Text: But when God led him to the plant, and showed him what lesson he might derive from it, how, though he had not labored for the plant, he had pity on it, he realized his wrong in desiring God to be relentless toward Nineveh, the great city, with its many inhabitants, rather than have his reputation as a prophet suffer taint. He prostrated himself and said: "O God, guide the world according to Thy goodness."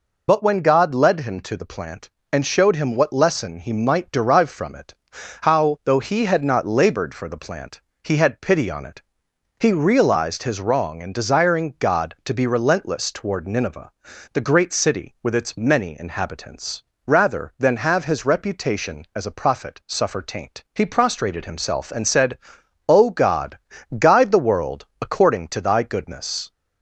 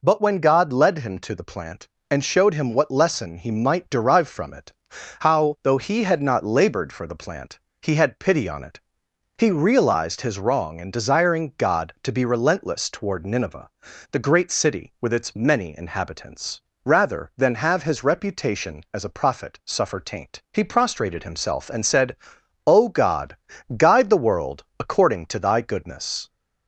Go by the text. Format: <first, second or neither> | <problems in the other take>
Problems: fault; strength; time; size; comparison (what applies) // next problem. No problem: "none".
second | loses the start of "But"; at 0.2 s; 35 ms // pauses between "world" and "according"; slight; at 24.8 s; 0.16 s long; slight in the second